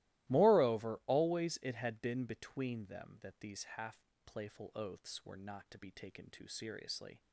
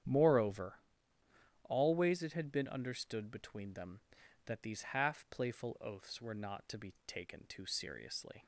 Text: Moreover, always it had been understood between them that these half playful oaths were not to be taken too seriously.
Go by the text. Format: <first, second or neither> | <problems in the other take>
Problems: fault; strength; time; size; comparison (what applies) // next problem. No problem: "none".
second | starts louder than the rest; strong; until 1.3 s; 16.5 dB; strong in the second // skips "understood"; at 2.2 s // pauses between "half" and "playful"; slight; at 3.9 s; 0.28 s long